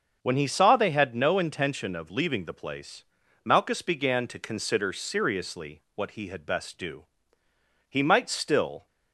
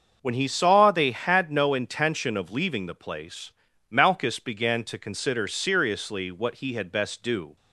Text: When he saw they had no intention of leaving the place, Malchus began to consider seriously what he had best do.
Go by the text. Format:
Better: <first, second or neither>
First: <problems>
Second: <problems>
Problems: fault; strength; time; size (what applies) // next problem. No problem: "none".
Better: second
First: starts louder than the rest; until 1.2 s; 6.5 dB // goes on to say "He might still"; noticeable; from 7.8 s on; 0.98 s long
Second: starts louder than the rest; until 1.2 s; 6.5 dB